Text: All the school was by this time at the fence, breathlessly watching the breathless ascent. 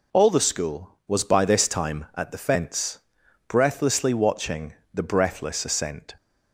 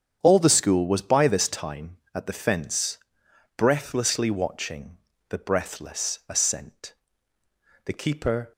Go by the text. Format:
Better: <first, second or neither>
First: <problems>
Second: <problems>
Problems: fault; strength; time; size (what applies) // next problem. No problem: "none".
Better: first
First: pauses between "watching" and "the"; slight; at 4.7 s; 0.20 s long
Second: starts louder than the rest; strong; until 1.2 s; 8 dB // pauses between "watching" and "the"; slight; at 4.9 s; 0.32 s long // goes on to say "The keeper"; noticeable; from 7.8 s on; 0.66 s long